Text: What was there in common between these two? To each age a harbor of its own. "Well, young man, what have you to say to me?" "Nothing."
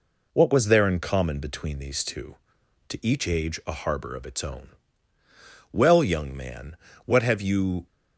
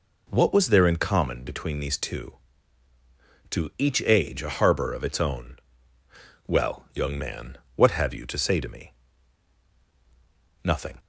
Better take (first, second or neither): second